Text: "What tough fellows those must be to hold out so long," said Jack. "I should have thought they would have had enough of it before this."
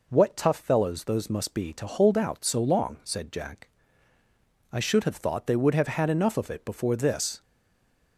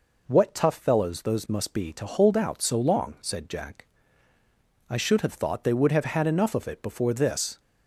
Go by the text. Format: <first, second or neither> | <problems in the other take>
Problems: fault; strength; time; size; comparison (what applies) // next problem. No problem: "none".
second | stays silent after the last word; slight; from 7.4 s on; 0.7 s long